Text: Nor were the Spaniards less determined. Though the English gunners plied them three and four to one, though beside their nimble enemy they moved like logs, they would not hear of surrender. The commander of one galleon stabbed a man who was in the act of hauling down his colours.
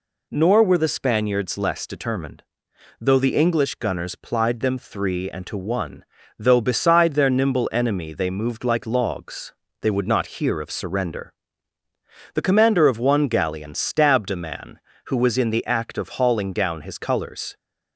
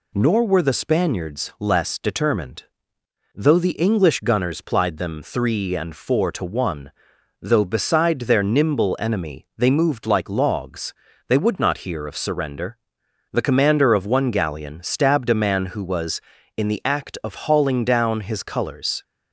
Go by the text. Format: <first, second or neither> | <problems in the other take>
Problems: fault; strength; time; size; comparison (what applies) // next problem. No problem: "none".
second | skips "four"; at 5.4 s